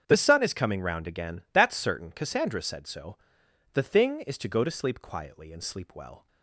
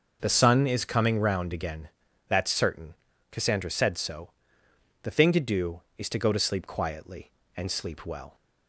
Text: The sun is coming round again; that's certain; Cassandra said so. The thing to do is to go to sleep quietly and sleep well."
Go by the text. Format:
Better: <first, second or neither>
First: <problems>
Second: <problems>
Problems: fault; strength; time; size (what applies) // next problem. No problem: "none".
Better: second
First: starts louder than the rest; strong; until 1.0 s; 7.5 dB // skips "to do"; at 4.2 s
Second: none